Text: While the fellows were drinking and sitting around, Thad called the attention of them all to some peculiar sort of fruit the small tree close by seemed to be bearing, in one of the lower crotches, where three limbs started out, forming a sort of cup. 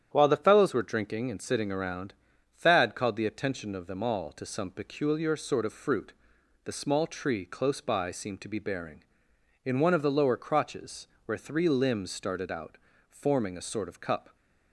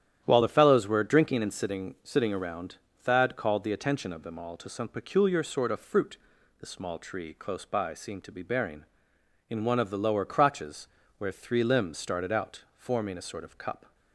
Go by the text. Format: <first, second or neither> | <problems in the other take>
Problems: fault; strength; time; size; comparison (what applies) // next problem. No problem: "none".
first | starts louder than the rest; strong; until 1.2 s; 10.5 dB; strong in the first // says "sitting" twice; at 2.0 s // pauses between "fruit" and "the"; at 6.1 s; 0.44 s long; noticeable in the first